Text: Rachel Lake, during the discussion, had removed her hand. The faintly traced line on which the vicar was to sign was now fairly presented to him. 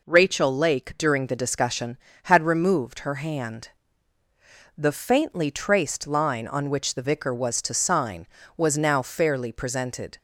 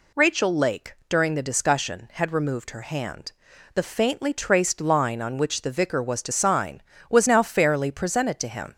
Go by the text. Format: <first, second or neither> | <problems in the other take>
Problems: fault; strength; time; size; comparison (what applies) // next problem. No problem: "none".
second | stops before "to him"; at 10.1 s